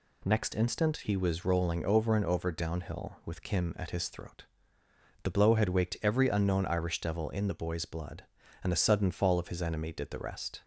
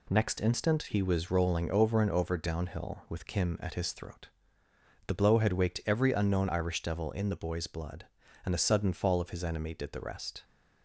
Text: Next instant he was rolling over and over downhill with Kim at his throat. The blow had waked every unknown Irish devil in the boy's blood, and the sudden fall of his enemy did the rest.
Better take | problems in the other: first | gets quieter; noticeable; throughout; 5 dB

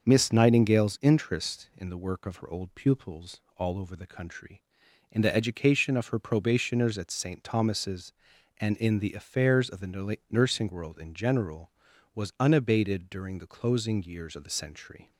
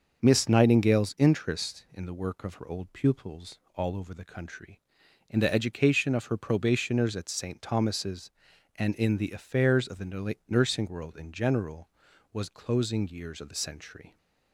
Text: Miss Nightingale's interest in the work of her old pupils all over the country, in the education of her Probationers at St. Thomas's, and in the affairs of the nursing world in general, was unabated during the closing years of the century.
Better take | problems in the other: first | starts louder than the rest; until 1.2 s; 6.5 dB; also in the first // pauses between "pupils" and "all"; slight; at 3.5 s; 0.16 s long; slight in the first // skips "unabated during the"; at 12.5 s

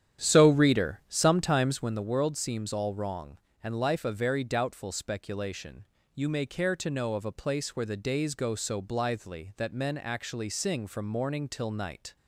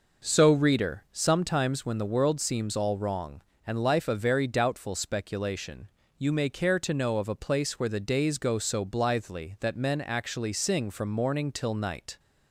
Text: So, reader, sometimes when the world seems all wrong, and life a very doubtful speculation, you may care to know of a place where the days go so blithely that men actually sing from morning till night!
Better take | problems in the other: second | starts louder than the rest; strong; until 2.0 s; 10 dB

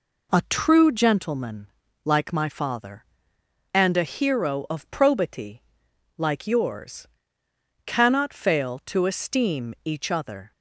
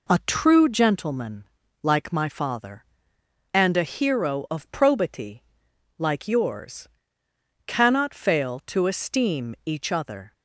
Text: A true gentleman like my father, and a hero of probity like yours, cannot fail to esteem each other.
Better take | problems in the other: neither | pauses between "gentleman" and "like"; the same in both // pauses between "probity" and "like"; noticeable; the same in both

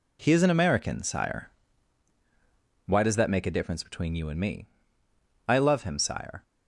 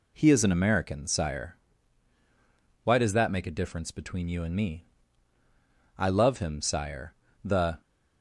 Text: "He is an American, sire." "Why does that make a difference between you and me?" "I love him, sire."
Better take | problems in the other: first | goes on to say "The"; slight; from 7.4 s on; 0.38 s long

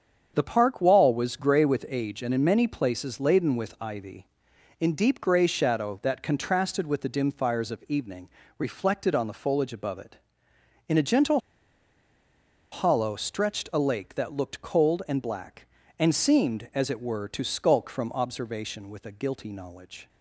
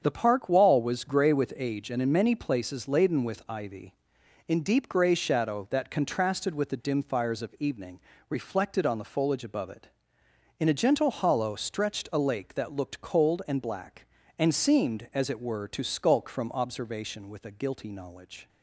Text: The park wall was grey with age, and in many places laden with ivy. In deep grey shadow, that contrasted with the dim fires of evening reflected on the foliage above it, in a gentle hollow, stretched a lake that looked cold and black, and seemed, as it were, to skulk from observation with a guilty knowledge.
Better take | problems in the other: second | starts louder than the rest; strong; until 1.3 s; 7.5 dB; strong in the second // pauses between "evening" and "reflected"; slight; at 8.2 s; 0.30 s long; slight in the second // pauses between "gentle" and "hollow"; strong; at 11.3 s; 1.3 s long

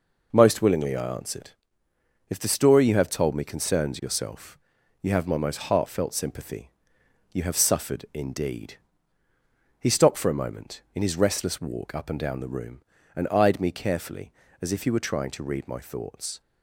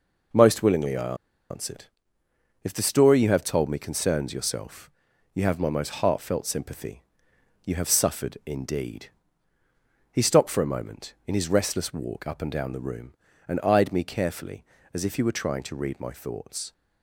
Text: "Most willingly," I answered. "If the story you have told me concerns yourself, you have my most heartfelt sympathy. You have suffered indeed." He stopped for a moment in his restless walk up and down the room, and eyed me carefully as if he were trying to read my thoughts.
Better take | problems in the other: first | pauses between "I" and "answered"; slight; at 1.1 s; 0.35 s long

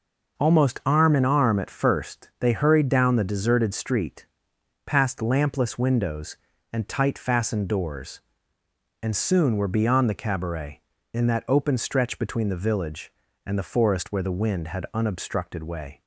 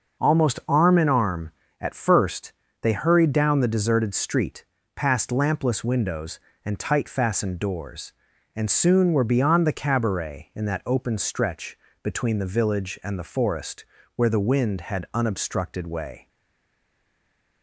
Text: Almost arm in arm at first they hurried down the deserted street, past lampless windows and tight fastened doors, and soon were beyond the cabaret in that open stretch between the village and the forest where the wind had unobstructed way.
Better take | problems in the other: first | starts louder than the rest; noticeable; until 1.2 s; 6 dB // pauses between "first" and "they"; slight; at 2.5 s; 0.28 s long // pauses between "stretch" and "between"; slight; at 11.7 s; 0.24 s long // pauses between "forest" and "where"; slight; at 13.8 s; 0.30 s long // stays silent after the last word; noticeable; from 16.2 s on; 1.4 s long

